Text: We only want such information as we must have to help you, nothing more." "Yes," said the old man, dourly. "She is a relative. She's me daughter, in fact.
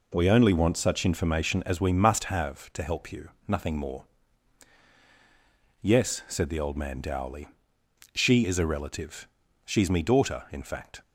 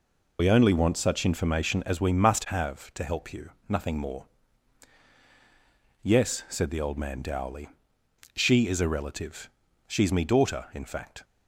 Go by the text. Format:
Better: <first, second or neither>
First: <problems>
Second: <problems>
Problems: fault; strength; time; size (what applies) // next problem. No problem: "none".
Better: first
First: none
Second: loses the start of "We"; at 0.3 s; 75 ms